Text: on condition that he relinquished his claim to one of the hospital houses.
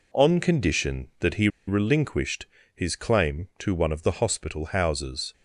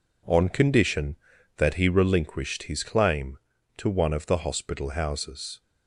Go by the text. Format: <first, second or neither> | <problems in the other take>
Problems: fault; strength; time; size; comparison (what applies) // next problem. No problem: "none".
second | pauses between "he" and "relinquished"; slight; at 1.4 s; 0.19 s long // pauses between "relinquished" and "his"; slight; at 2.4 s; 0.30 s long